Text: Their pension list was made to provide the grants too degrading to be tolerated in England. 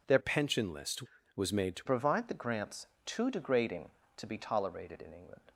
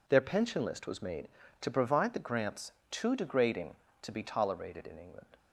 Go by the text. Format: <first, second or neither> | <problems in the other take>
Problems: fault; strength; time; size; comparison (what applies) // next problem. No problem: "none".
second | changes voice from "pension" to "to"; from 0.1 to 1.8 s; 1.7 s long // pauses between "grants" and "too"; slight; at 2.8 s; 0.18 s long; slight in the second